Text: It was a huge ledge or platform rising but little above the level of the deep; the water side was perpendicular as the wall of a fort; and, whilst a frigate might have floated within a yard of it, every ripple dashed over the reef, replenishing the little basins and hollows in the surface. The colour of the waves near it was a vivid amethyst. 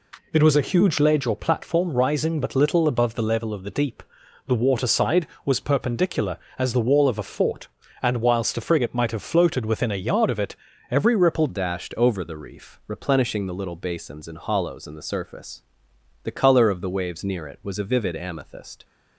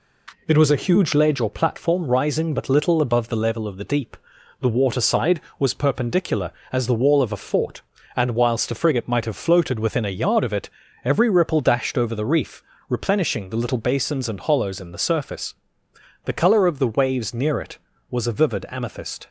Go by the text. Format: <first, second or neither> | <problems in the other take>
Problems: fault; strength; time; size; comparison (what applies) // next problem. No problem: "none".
second | changes voice at "dashed"; from 11.4 s on; 7.4 s long